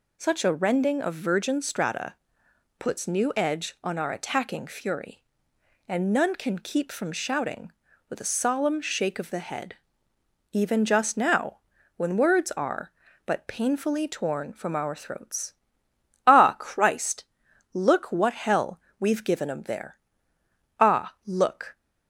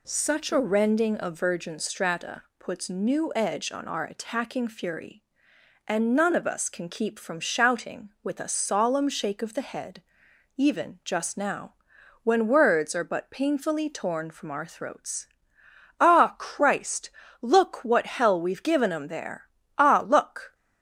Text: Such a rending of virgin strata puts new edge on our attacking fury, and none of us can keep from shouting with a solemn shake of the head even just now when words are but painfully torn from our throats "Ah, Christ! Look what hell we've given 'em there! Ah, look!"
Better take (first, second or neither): second